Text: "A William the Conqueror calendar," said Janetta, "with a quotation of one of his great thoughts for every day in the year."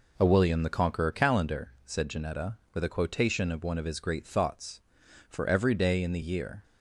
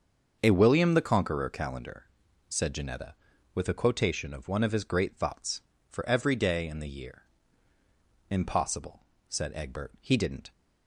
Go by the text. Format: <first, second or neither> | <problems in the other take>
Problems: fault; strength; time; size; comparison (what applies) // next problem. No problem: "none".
first | starts louder than the rest; until 1.4 s; 6.5 dB // goes on to say "Impossible said Egbert he didn't"; strong; from 8.2 s on; 2.2 s long